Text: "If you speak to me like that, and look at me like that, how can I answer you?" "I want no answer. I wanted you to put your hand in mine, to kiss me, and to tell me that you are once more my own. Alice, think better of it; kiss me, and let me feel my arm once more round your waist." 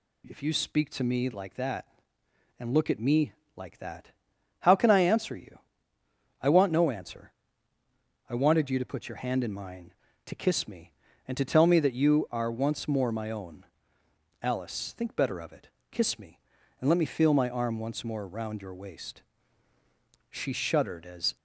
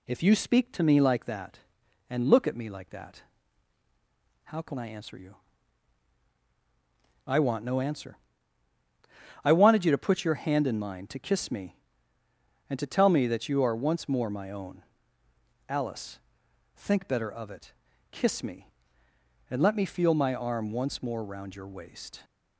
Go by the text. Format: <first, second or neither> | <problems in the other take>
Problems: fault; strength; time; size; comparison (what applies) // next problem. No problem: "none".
second | pauses between "me" and "like"; slight; at 3.3 s; 0.24 s long // goes on to say "She shuddered as"; noticeable; from 20.3 s on; 1.0 s long